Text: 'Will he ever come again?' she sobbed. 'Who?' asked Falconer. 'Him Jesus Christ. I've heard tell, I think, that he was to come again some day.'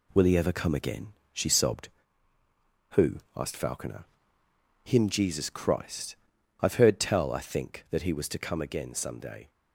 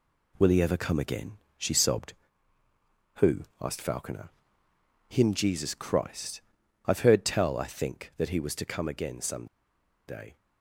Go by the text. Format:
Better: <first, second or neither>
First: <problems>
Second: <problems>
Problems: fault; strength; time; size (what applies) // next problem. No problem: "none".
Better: first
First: none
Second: pauses between "some" and "day"; noticeable; at 9.4 s; 0.61 s long